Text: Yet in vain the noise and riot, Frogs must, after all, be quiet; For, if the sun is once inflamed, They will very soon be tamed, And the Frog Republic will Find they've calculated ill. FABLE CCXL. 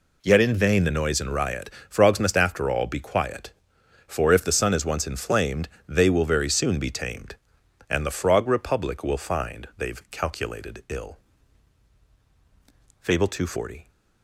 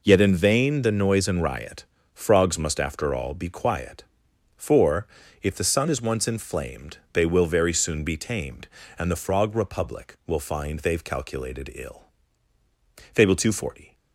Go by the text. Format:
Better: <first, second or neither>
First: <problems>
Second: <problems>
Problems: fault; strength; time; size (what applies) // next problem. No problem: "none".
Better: neither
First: none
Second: none